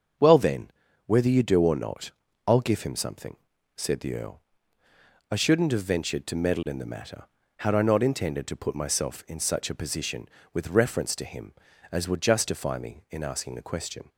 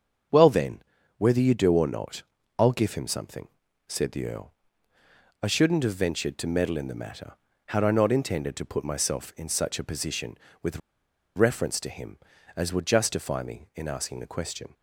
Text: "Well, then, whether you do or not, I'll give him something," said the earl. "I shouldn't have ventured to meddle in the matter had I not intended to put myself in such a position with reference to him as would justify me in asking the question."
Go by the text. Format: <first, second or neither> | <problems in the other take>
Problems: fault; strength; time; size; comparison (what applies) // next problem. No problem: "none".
first | starts louder than the rest; until 1.6 s; 6.5 dB; also in the first // pauses between "with" and "reference"; noticeable; at 10.7 s; 0.56 s long